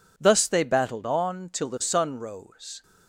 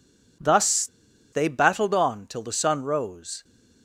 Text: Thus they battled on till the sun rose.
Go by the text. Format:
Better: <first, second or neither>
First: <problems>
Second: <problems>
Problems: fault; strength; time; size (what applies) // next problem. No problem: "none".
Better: first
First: none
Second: pauses between "Thus" and "they"; noticeable; at 0.8 s; 0.46 s long